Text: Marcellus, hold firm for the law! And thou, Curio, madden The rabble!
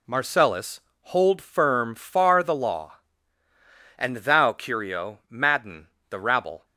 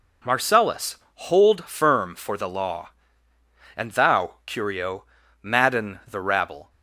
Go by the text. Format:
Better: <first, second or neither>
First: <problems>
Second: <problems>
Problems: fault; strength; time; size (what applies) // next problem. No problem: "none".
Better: second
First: says "far" for "for"; at 1.9 s // pauses between "madden" and "The"; slight; at 5.8 s; 0.24 s long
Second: none